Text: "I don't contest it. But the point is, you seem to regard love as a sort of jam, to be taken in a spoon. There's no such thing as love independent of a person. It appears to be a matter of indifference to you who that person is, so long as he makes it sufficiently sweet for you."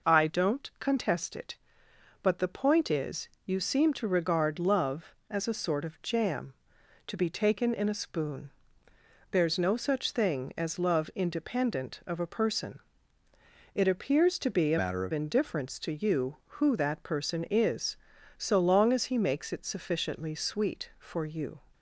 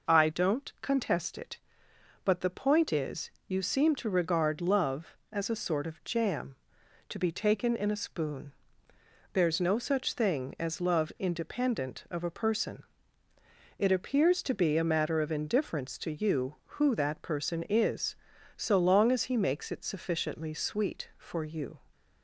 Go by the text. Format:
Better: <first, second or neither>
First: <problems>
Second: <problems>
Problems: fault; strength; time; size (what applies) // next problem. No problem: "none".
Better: second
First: changes voice from "matter" to "of"; from 14.7 to 15.1 s; 0.4 s long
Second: none